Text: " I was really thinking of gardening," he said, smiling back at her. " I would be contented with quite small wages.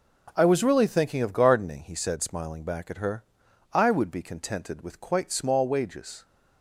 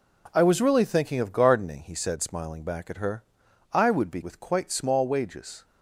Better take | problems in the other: first | skips "contented"; at 4.2 s

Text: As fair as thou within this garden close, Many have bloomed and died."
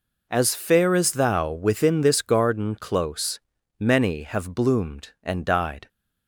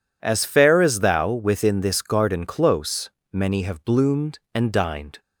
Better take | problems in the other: first | says "dined" for "died"; at 4.7 s

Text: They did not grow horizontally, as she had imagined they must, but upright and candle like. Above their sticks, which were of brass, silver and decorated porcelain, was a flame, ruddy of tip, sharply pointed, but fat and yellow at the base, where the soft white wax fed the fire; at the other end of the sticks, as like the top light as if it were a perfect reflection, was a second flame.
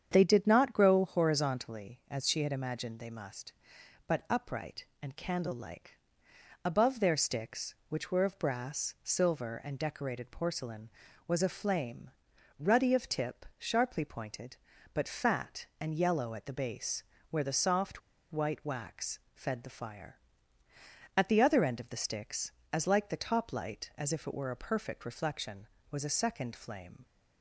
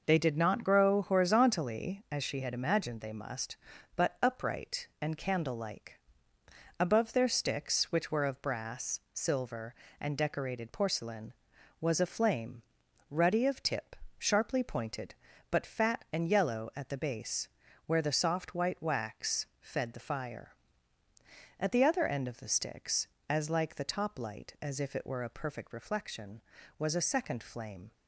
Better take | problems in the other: second | starts louder than the rest; strong; until 1.1 s; 8 dB // pauses between "soft" and "white"; slight; at 18.0 s; 0.31 s long // pauses between "wax" and "fed"; slight; at 19.2 s; 0.16 s long

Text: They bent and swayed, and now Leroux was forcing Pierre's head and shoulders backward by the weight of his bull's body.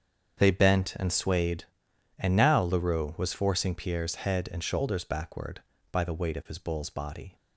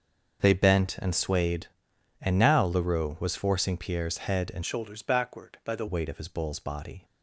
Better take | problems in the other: first | starts louder than the rest; until 1.4 s; 6.5 dB; strong in the first // changes voice from "shoulders" to "the"; from 4.6 to 5.8 s; 1.2 s long

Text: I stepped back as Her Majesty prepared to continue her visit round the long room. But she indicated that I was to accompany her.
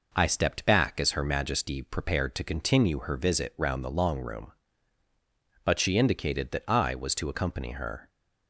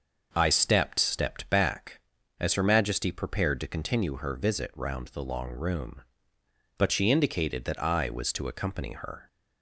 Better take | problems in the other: first | starts louder than the rest; noticeable; until 1.3 s; 6 dB // says "stepped" twice; at 0.9 s

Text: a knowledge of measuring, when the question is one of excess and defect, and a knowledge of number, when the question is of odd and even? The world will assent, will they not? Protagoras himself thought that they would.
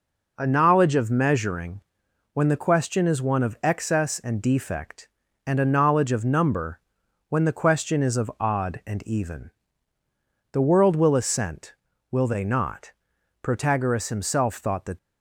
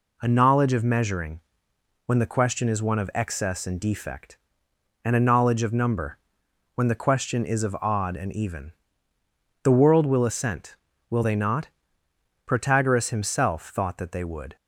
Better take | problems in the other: second | stops before "they would"; at 14.9 s

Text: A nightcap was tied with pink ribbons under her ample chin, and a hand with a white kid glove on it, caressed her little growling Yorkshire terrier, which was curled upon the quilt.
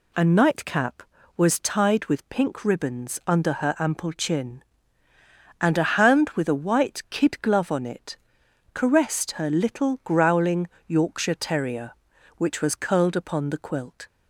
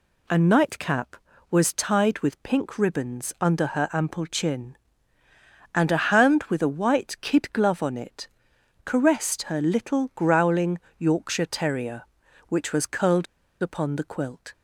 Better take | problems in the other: first | pauses between "growling" and "Yorkshire"; slight; at 10.7 s; 0.18 s long; slight in the first // pauses between "curled" and "upon"; at 13.2 s; 0.36 s long

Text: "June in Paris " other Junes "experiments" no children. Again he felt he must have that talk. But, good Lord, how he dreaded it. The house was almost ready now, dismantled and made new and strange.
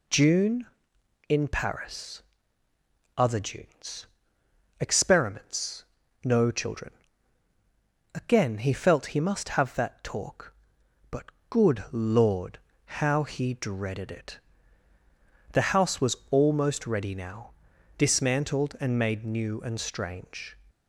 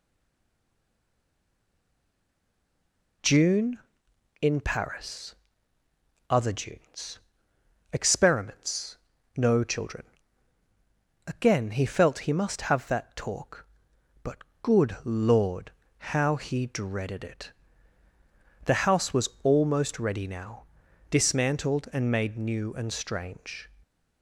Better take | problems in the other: first | stays silent before the first word; strong; until 3.2 s; 3.2 s long // pauses between "Junes" and "experiments"; noticeable; at 7.1 s; 0.74 s long; noticeable in the first // pauses between "experiments" and "no"; at 8.9 s; 0.40 s long; also in the first

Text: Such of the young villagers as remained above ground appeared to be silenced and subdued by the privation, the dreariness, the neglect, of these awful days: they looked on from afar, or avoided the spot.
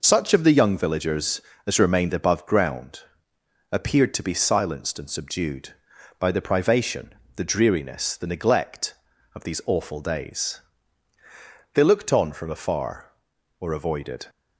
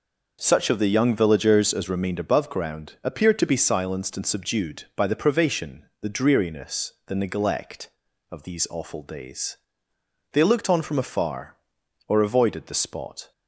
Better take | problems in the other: second | pauses between "ground" and "appeared"; noticeable; at 3.0 s; 0.70 s long // stops before "the spot"; at 14.2 s

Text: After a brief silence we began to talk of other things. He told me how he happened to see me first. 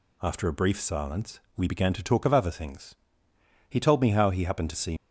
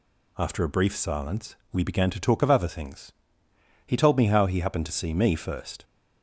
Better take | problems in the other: second | pauses between "silence" and "we"; slight; at 1.4 s; 0.16 s long; slight in the second // stops before "me first"; at 4.9 s

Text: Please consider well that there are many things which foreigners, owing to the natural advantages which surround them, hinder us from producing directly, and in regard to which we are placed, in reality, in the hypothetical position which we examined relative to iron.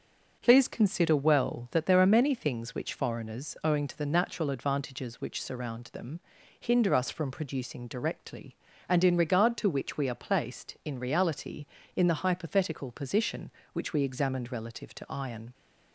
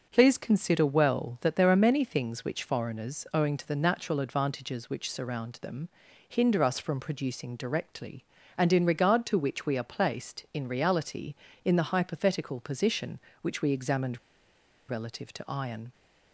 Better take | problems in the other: first | starts louder than the rest; until 1.1 s; 6.5 dB; also in the first // pauses between "examined" and "relative"; noticeable; at 14.1 s; 0.71 s long

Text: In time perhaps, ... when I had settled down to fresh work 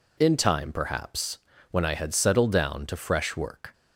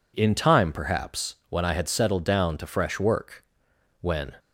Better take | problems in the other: first | goes on to say "when"; slight; from 4.0 s on; 0.36 s long

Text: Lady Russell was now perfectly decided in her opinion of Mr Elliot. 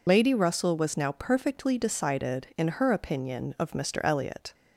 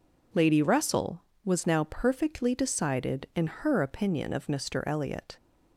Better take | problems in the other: second | loses the start of "Lady"; at 0.0 s; 55 ms

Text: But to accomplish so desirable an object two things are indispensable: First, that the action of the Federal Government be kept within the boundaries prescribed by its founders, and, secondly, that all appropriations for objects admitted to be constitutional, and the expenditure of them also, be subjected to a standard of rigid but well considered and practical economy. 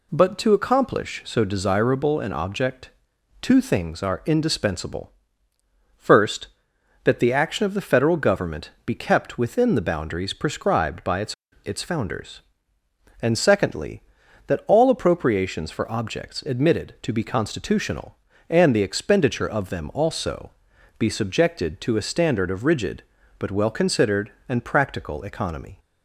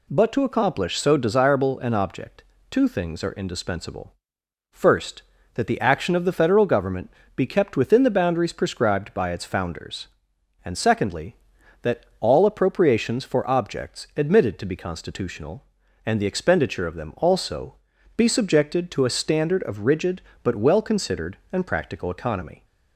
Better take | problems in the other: second | pauses between "object" and "two"; noticeable; at 2.8 s; 0.52 s long; slight in the second // pauses between "Government" and "be"; slight; at 8.7 s; 0.16 s long; slight in the second // says "its" twice; at 11.6 s

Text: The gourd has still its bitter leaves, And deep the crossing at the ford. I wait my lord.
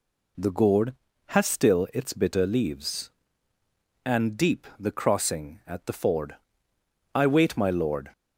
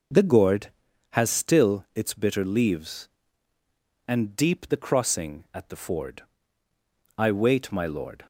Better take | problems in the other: neither | none

